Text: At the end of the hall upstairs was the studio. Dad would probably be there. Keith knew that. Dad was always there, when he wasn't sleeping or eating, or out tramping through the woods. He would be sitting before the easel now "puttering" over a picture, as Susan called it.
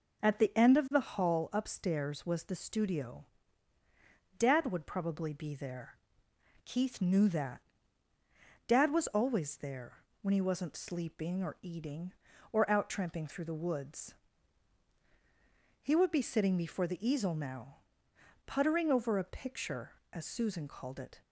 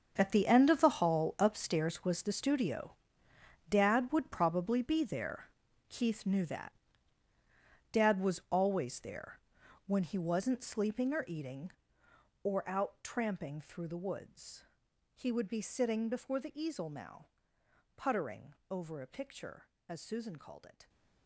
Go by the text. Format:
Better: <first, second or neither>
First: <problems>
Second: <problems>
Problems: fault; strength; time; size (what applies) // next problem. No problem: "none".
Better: first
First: pauses between "now" and "puttering"; noticeable; at 17.7 s; 0.68 s long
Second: gets quieter; strong; throughout; 14.5 dB // pauses between "now" and "puttering"; noticeable; at 17.2 s; 0.72 s long // pauses between "puttering" and "over"; slight; at 18.5 s; 0.16 s long